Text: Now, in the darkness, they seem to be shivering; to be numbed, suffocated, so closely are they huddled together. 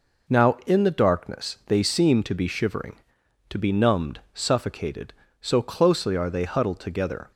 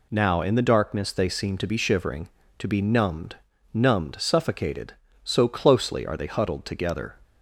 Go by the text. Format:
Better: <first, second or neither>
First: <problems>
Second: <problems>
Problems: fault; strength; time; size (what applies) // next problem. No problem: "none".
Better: first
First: none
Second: says "numbed" twice; at 3.7 s